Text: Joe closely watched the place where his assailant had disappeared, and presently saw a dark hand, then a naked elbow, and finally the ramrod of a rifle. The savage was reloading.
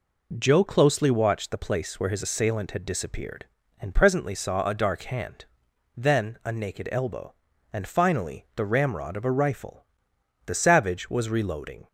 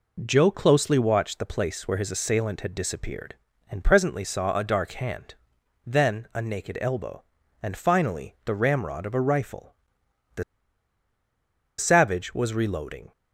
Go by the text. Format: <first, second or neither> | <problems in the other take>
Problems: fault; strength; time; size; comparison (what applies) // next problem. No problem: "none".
first | pauses between "The" and "savage"; strong; at 10.4 s; 1.3 s long